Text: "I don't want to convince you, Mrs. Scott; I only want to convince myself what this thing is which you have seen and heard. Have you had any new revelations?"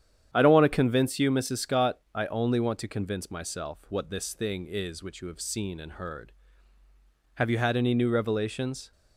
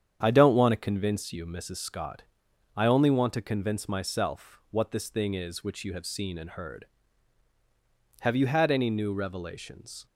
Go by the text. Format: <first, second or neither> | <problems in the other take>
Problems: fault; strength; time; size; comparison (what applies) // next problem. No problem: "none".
neither | starts louder than the rest; strong; the same in both